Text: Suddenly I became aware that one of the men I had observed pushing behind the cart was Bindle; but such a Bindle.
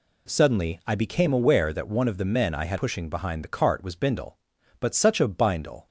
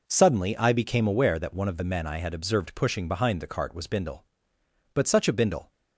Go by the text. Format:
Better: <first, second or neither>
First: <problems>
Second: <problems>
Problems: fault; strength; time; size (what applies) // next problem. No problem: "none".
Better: second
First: skips "observed"; at 2.7 s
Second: none